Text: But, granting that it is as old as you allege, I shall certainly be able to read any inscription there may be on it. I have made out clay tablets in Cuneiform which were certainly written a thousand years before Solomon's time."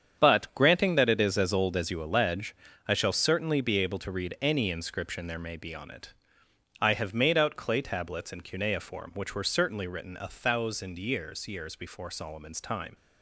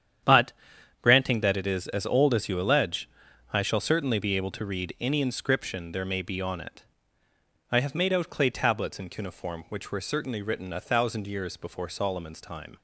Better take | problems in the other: second | starts louder than the rest; strong; until 1.2 s; 8 dB; strong in the second // says "years" twice; at 11.4 s

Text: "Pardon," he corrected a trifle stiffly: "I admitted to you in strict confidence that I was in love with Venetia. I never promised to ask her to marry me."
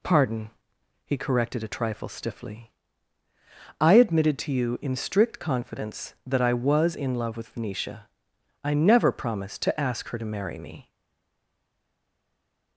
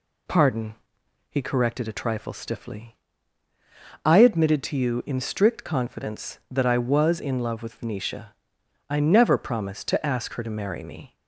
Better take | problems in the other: second | stays silent after the last word; noticeable; from 10.8 s on; 1.9 s long

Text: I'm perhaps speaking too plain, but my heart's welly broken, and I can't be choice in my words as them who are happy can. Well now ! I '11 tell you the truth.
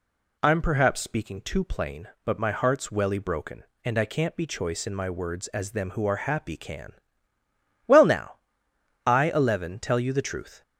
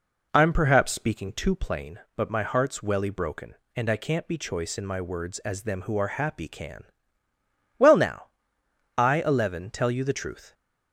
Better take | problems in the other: first | starts louder than the rest; noticeable; until 1.8 s; 4 dB

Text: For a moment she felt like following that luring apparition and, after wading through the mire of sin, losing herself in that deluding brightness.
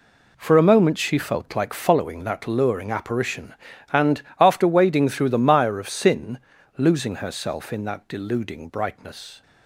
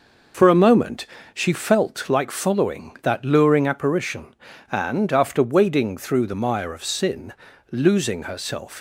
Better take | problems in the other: first | pauses between "moment" and "she"; slight; at 1.0 s; 0.28 s long // stops before "in that deluding brightness"; at 8.7 s

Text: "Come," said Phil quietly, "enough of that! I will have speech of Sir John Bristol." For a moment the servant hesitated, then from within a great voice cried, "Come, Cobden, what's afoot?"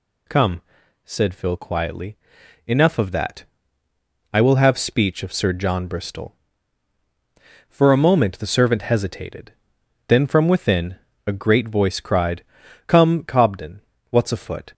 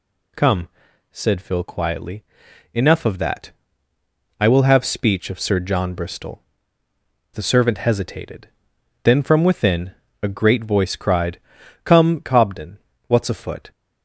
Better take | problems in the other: first | skips "For a moment"; at 6.8 s // pauses between "within" and "a"; slight; at 9.9 s; 0.30 s long; slight in the first

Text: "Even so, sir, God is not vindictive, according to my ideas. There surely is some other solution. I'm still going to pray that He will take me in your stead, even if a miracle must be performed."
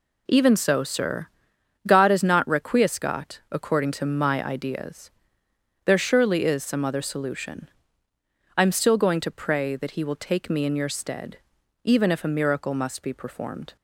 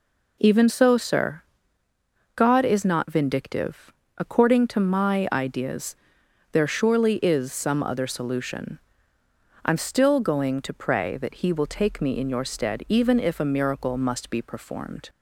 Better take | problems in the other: second | says "requiescat" for "vindictive"; at 2.4 s

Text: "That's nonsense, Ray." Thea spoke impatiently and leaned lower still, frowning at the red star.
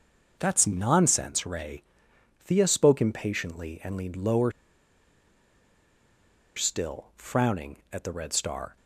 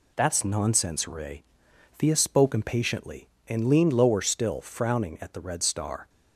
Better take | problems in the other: second | starts louder than the rest; until 1.4 s; 6 dB // pauses between "lower" and "still"; strong; at 4.5 s; 2.0 s long

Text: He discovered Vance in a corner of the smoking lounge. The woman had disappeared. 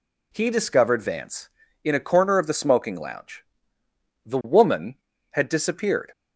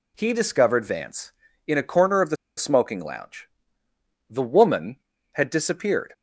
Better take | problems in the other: first | pauses between "the" and "smoking"; slight; at 2.3 s; 0.22 s long

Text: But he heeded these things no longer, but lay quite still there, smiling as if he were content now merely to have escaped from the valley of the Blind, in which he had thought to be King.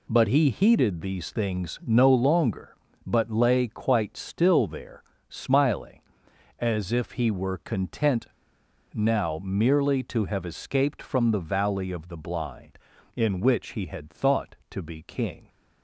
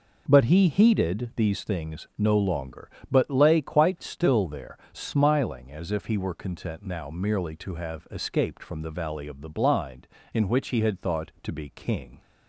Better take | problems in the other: second | pauses between "content" and "now"; noticeable; at 8.2 s; 0.65 s long

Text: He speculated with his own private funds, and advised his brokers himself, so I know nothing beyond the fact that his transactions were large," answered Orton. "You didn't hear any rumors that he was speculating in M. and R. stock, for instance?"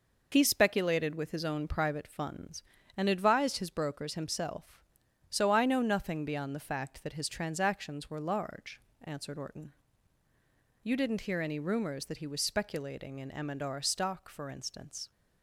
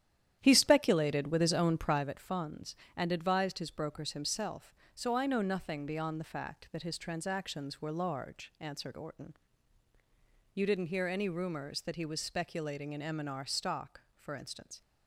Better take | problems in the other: first | starts louder than the rest; strong; until 2.1 s; 10.5 dB

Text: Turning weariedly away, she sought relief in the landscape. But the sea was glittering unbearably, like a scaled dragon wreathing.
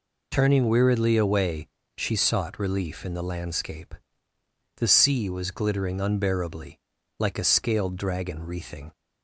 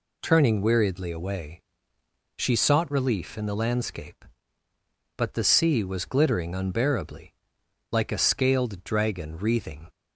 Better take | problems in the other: second | skips "But"; at 4.3 s

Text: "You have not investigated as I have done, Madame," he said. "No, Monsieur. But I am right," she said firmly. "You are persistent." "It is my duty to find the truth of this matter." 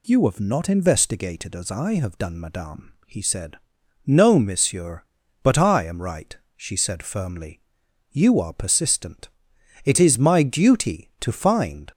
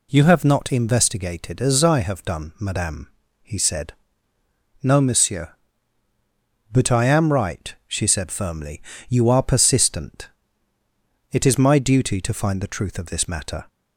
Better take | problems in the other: second | stops before "the truth of this matter"; at 11.9 s

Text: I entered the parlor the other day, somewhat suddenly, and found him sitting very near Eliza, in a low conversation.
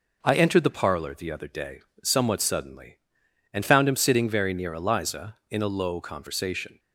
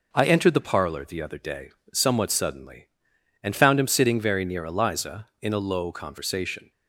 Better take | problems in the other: neither | none

